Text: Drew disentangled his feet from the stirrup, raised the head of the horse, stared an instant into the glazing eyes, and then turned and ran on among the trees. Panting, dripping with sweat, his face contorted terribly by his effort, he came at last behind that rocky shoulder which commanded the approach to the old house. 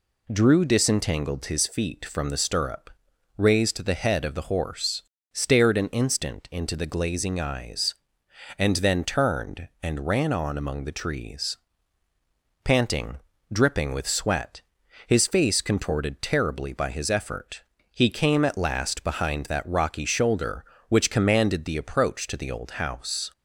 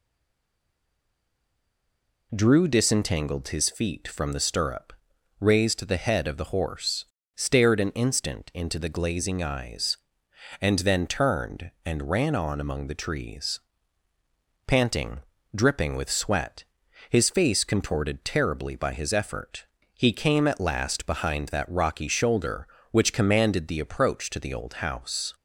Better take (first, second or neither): first